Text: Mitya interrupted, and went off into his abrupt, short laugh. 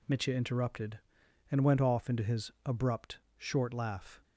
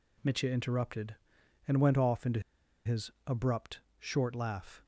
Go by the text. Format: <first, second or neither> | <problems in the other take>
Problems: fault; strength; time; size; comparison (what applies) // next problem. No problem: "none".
first | pauses between "into" and "his"; at 2.4 s; 0.44 s long // pauses between "his" and "abrupt"; slight; at 3.0 s; 0.16 s long